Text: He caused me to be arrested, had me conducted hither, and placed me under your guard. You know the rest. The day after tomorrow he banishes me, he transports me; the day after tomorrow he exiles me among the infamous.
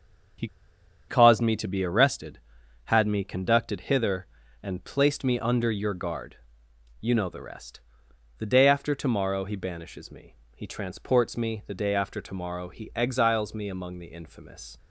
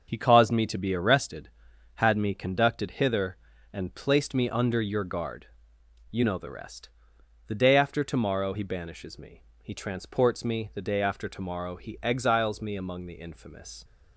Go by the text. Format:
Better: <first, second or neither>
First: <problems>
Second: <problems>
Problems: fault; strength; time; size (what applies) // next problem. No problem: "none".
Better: second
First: starts louder than the rest; until 2.0 s; 6.5 dB // pauses between "He" and "caused"; noticeable; at 0.4 s; 0.61 s long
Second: none